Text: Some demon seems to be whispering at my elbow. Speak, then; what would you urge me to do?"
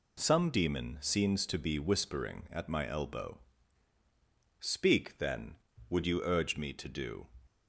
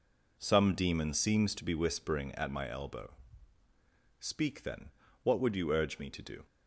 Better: second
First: skips "what"; at 5.7 s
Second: none

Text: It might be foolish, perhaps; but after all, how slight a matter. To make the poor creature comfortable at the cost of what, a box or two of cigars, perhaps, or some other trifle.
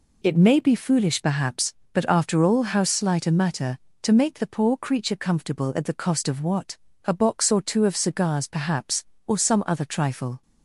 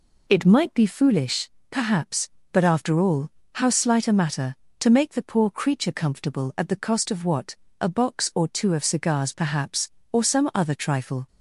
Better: second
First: says "may" for "might"; at 0.3 s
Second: none

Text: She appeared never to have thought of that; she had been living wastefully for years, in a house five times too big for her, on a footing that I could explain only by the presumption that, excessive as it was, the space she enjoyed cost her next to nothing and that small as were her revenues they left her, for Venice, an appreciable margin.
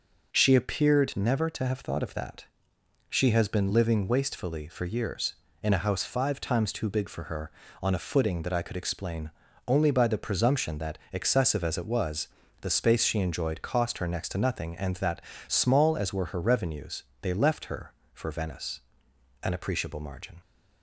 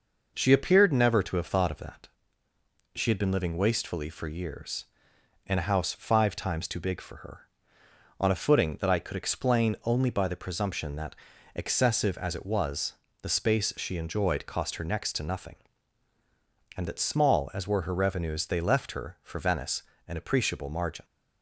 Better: second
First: says "has" for "had"; at 3.3 s // pauses between "explain" and "only"; slight; at 9.3 s; 0.34 s long // pauses between "that" and "small"; slight; at 15.2 s; 0.26 s long // pauses between "revenues" and "they"; slight; at 17.0 s; 0.20 s long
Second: none

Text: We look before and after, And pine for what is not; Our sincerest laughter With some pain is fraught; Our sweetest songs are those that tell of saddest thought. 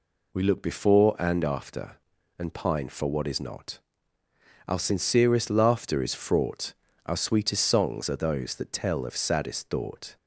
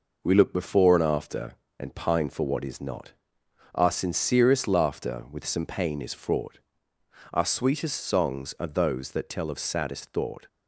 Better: second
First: skips "With some pain"; at 6.0 s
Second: none

